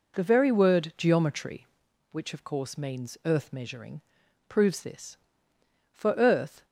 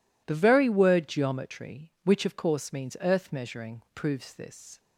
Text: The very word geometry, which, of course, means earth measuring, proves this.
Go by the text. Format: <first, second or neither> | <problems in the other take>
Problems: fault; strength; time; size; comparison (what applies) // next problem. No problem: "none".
second | goes on to say "For earth"; noticeable; from 5.9 s on; 0.74 s long